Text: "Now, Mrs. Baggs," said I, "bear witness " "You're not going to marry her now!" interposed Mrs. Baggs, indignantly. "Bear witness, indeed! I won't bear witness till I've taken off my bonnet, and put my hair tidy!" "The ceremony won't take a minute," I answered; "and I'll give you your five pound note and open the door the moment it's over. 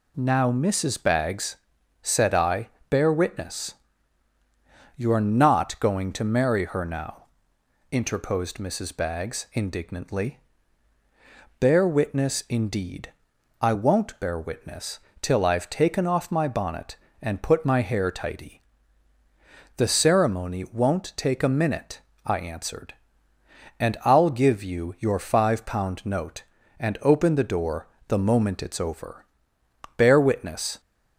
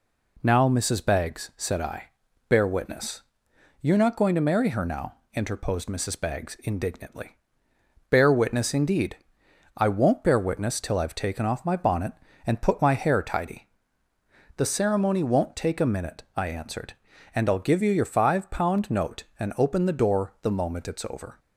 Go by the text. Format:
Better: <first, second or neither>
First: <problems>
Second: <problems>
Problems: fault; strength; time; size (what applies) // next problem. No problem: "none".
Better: second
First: pauses between "witness" and "till"; slight; at 14.9 s; 0.20 s long // pauses between "door" and "the"; slight; at 27.8 s; 0.18 s long // goes on to say "Bear witness"; noticeable; from 29.9 s on; 0.84 s long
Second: none